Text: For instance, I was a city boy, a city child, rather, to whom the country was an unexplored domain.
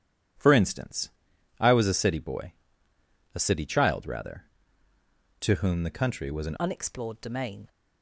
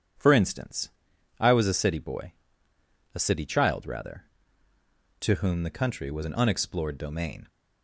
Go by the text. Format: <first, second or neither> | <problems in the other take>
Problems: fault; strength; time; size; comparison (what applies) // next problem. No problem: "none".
second | starts louder than the rest; strong; until 1.8 s; 11 dB; strong in the second // changes voice at "unexplored"; from 6.5 s on; 1.1 s long